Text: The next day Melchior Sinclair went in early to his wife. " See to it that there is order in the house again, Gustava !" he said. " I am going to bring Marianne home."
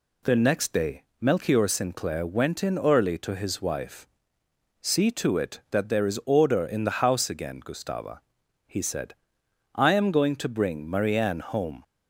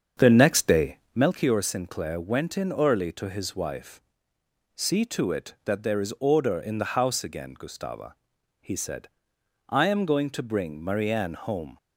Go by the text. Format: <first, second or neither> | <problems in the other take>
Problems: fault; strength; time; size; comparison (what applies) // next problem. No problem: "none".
first | starts louder than the rest; strong; until 1.4 s; 9 dB // pauses between "day" and "Melchior"; slight; at 0.9 s; 0.16 s long; slight in the first